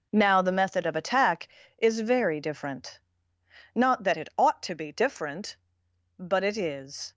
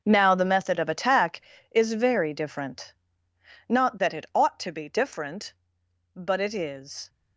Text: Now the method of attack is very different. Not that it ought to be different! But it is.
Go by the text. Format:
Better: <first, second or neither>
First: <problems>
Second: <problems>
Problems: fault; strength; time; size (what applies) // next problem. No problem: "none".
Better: first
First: none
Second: gets quieter; strong; throughout; 13 dB